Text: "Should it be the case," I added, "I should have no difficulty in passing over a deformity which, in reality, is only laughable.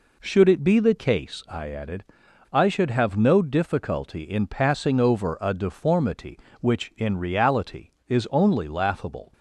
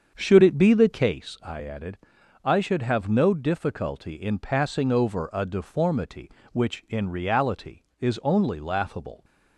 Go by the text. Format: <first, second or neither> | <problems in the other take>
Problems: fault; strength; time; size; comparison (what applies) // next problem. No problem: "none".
first | starts louder than the rest; until 1.1 s; 7 dB